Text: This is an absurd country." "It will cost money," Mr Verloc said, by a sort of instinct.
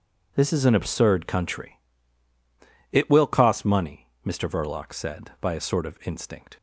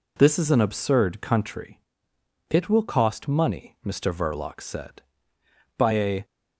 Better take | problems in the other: first | stops before "sort of instinct"; at 6.2 s

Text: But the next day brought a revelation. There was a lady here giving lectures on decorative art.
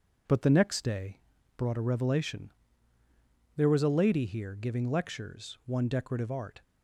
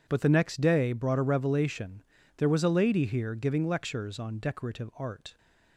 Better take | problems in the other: second | pauses between "day" and "brought"; slight; at 1.1 s; 0.36 s long // says "one" for "on"; at 5.6 s

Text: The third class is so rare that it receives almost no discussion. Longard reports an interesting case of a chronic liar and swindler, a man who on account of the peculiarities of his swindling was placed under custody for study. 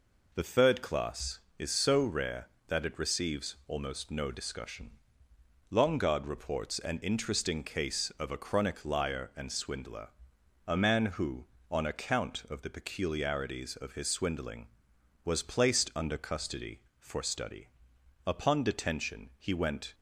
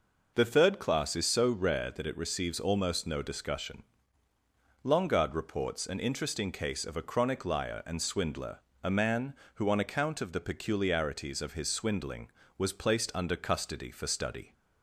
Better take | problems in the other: second | goes on to say "Upon detention he went"; strong; from 18.2 s on; 1.6 s long

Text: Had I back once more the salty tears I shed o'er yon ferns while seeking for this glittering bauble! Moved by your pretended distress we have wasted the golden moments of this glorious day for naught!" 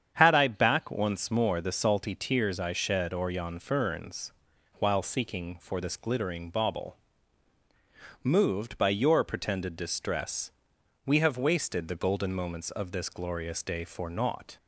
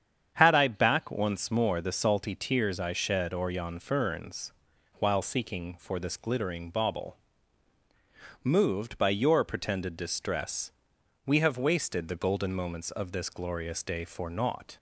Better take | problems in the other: neither | starts louder than the rest; strong; the same in both // pauses between "ferns" and "while"; noticeable; the same in both // pauses between "distress" and "we"; noticeable; the same in both

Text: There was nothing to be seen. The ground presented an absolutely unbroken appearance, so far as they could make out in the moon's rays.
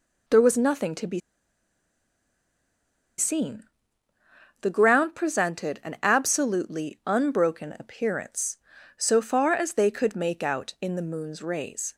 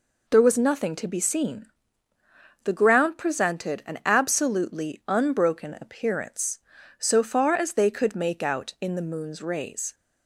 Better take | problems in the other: second | pauses between "be" and "seen"; strong; at 1.2 s; 1.9 s long

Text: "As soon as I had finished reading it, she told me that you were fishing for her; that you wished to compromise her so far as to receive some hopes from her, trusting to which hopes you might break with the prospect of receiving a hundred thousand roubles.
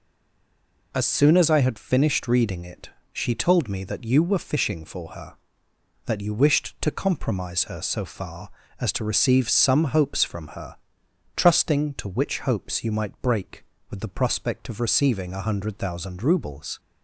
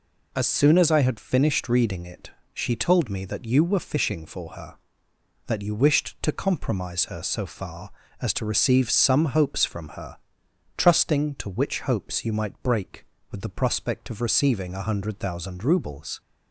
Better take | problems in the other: second | stays silent before the first word; slight; until 0.9 s; 0.9 s long

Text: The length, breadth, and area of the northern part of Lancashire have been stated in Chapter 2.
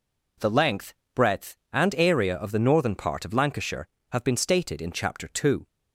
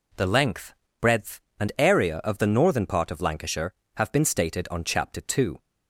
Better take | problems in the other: first | says "on" for "in"; at 4.6 s

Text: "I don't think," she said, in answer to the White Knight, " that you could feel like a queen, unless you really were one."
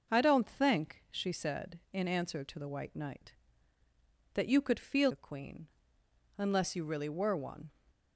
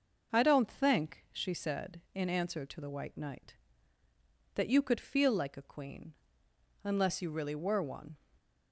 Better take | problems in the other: second | starts louder than the rest; until 1.1 s; 6 dB; also in the second // skips "like"; at 5.1 s

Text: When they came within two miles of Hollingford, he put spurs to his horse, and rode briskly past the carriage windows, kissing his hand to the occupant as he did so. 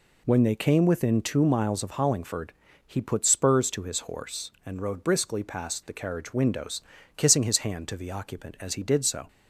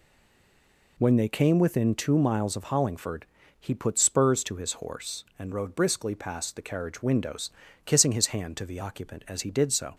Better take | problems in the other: first | stays silent before the first word; until 0.9 s; 0.9 s long

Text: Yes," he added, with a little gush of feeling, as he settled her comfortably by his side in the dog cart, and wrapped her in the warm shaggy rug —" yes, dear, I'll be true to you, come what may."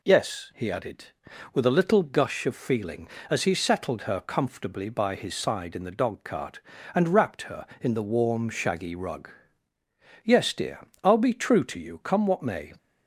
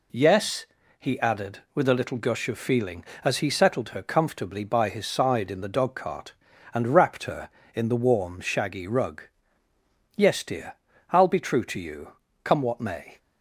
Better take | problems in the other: neither | none

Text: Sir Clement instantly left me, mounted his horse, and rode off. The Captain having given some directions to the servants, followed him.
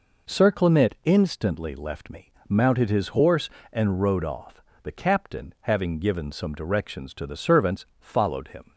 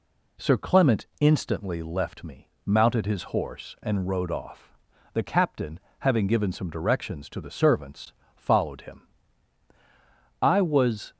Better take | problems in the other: first | pauses between "Captain" and "having"; slight; at 5.7 s; 0.20 s long // goes on to say "I was"; noticeable; from 10.4 s on; 0.70 s long

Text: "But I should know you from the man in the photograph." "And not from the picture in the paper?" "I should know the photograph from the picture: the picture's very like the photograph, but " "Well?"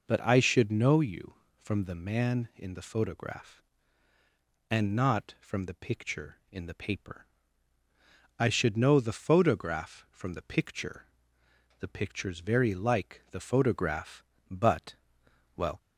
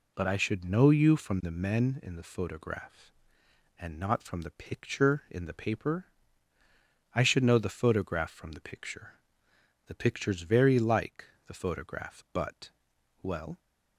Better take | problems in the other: first | says "men" for "man"; at 1.5 s // pauses between "like" and "the"; slight; at 11.2 s; 0.22 s long

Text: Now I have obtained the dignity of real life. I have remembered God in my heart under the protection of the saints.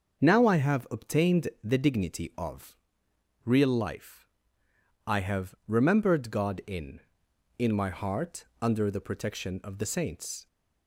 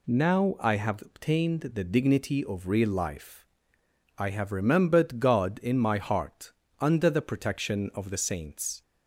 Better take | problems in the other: second | starts louder than the rest; until 1.2 s; 6.5 dB // pauses between "obtained" and "the"; slight; at 1.4 s; 0.16 s long // pauses between "of" and "real"; noticeable; at 2.7 s; 0.70 s long // says "in" twice; at 7.5 s // pauses between "heart" and "under"; slight; at 8.4 s; 0.18 s long; slight in the second

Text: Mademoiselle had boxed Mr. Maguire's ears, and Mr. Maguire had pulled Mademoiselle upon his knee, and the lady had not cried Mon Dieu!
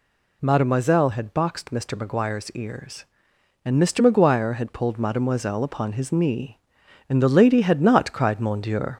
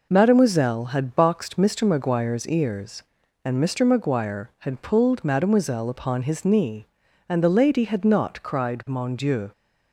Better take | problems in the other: second | gets louder; slight; throughout; 3 dB

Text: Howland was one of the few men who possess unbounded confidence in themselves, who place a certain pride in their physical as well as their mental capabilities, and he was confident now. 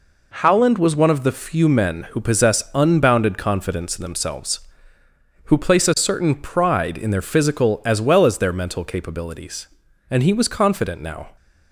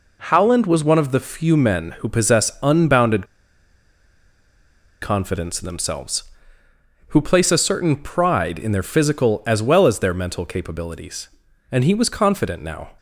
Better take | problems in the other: first | pauses between "unbounded" and "confidence"; strong; at 3.2 s; 1.7 s long

